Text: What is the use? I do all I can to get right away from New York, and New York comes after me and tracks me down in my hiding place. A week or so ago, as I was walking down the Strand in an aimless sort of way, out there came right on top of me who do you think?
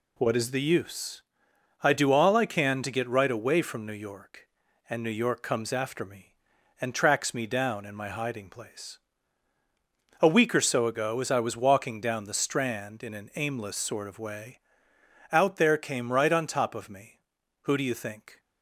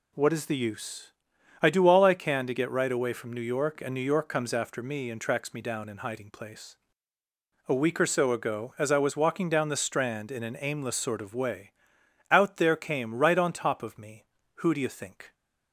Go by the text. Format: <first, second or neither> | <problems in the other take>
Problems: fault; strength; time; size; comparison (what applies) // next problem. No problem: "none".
first | skips "my"; at 5.9 s